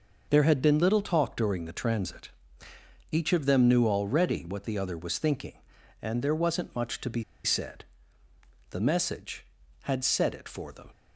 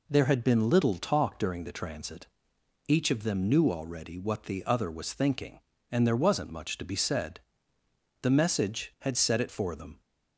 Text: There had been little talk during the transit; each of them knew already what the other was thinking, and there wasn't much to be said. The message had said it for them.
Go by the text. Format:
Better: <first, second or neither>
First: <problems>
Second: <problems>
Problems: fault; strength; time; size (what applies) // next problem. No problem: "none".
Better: second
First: pauses between "be" and "said"; slight; at 7.2 s; 0.20 s long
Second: none